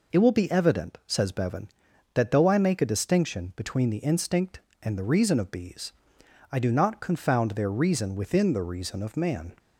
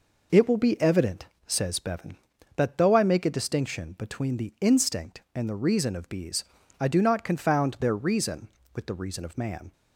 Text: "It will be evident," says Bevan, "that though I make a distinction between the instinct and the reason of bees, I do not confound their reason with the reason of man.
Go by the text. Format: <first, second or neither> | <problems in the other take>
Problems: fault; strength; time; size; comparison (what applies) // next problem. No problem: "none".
second | says "within" for "with"; at 8.1 s